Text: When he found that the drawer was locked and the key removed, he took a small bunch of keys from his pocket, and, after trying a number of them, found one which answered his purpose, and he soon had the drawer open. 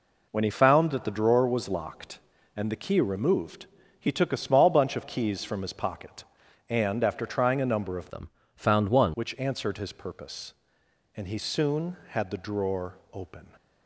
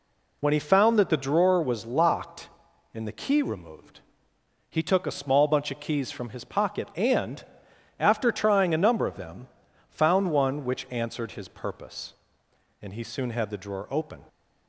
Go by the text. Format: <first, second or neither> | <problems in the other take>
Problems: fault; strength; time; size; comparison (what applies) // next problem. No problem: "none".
second | changes voice from "them" to "one"; from 8.0 to 9.1 s; 1.1 s long // pauses between "drawer" and "open"; slight; at 12.9 s; 0.16 s long